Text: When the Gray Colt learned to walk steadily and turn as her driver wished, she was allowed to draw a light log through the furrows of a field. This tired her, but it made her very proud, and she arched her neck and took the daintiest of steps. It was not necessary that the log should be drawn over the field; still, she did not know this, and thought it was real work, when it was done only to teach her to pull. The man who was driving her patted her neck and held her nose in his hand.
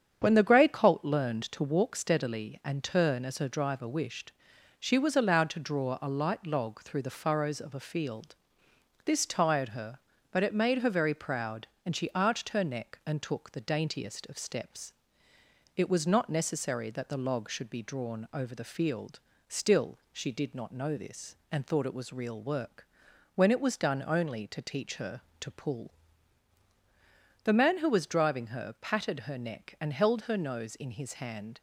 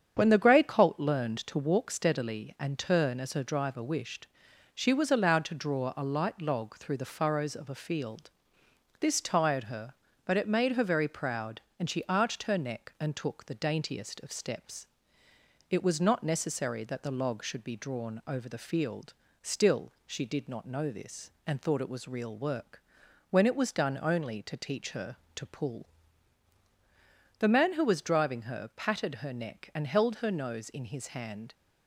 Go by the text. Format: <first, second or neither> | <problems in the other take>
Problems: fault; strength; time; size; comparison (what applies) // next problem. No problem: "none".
neither | starts louder than the rest; strong; the same in both